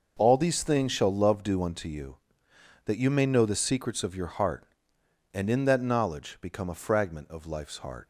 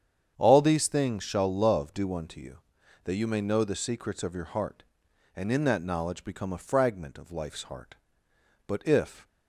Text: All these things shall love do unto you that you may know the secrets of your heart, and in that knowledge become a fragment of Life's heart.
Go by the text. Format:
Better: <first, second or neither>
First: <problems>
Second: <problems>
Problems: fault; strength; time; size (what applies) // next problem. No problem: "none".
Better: first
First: none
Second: starts louder than the rest; strong; until 1.3 s; 8 dB // goes on to say "But if"; noticeable; from 8.6 s on; 0.62 s long